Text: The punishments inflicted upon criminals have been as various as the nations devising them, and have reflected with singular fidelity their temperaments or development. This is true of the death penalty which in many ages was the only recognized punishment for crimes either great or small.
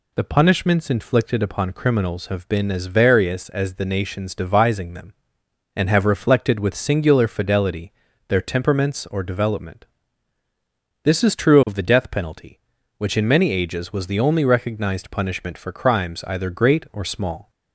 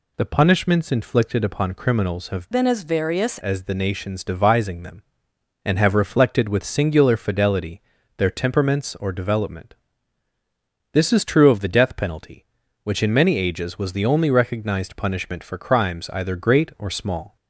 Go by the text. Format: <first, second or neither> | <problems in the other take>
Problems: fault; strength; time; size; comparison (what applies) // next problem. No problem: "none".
first | changes voice from "been" to "various"; from 2.5 to 3.3 s; 0.8 s long // pauses between "fidelity" and "their"; slight; at 7.8 s; 0.34 s long; slight in the first